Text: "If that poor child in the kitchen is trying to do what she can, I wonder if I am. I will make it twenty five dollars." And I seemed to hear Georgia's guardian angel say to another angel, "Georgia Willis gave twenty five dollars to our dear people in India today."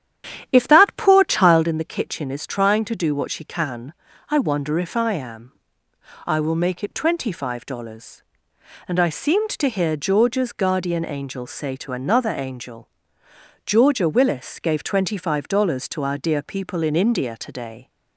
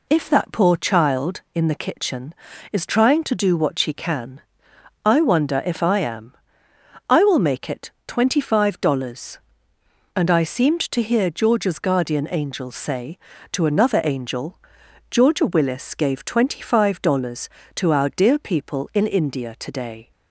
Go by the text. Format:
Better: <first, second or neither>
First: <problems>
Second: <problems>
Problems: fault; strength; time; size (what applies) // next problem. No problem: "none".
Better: second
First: starts louder than the rest; strong; until 1.7 s; 10 dB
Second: none